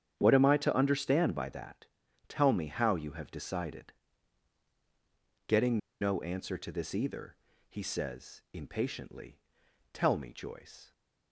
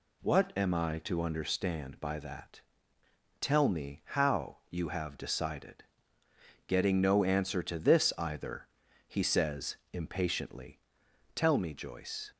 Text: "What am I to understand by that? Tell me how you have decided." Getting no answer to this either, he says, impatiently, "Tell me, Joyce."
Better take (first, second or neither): second